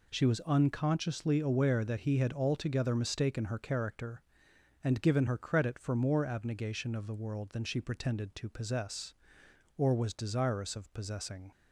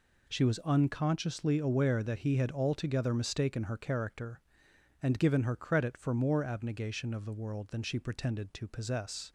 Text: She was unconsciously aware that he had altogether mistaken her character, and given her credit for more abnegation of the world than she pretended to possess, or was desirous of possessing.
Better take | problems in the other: first | stops before "or was desirous of possessing"; at 9.2 s

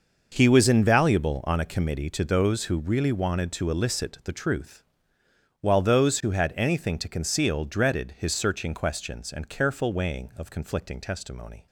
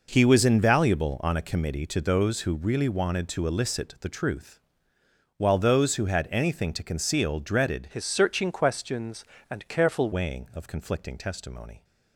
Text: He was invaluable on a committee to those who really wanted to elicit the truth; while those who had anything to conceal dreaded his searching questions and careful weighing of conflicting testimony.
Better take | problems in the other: first | changes voice from "his" to "careful"; from 7.9 to 10.1 s; 2.2 s long

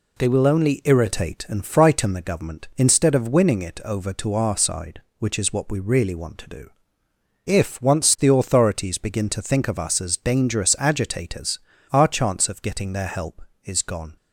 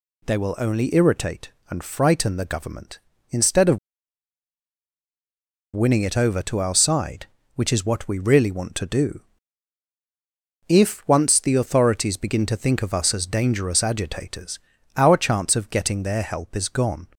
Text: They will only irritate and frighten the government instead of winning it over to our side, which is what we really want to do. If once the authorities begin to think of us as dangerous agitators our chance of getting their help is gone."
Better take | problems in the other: first | pauses between "of" and "winning"; strong; at 3.7 s; 1.9 s long // pauses between "agitators" and "our"; at 14.5 s; 0.38 s long; slight in the first

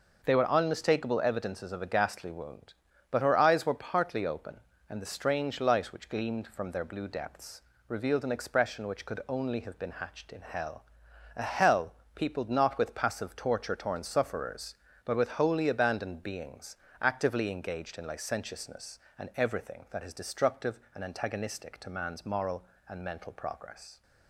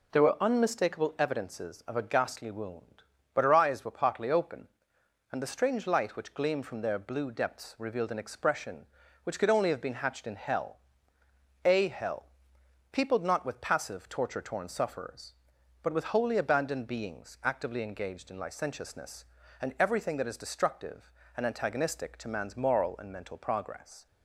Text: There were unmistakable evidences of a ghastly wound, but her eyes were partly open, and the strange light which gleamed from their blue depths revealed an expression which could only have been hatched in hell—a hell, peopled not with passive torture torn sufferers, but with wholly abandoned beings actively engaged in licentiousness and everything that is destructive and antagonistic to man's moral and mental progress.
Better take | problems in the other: second | says "They" for "There"; at 0.2 s // pauses between "depths" and "revealed"; slight; at 7.6 s; 0.26 s long // pauses between "beings" and "actively"; slight; at 16.7 s; 0.24 s long

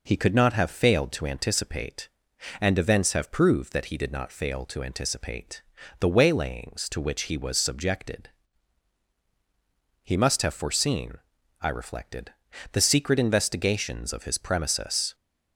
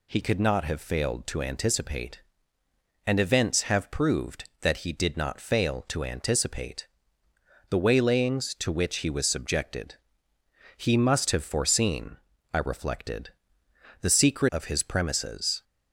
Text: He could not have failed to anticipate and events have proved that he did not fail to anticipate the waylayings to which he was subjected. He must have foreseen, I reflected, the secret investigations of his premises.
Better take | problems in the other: first | pauses between "anticipate" and "the"; noticeable; at 6.8 s; 0.82 s long; slight in the first // skips "investigations"; at 14.5 s

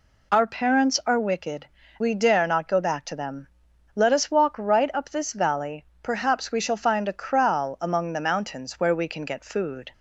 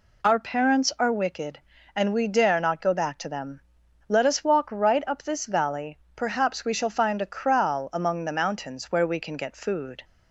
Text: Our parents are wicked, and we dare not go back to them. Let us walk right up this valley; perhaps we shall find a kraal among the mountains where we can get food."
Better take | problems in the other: second | skips "and"; at 1.8 s

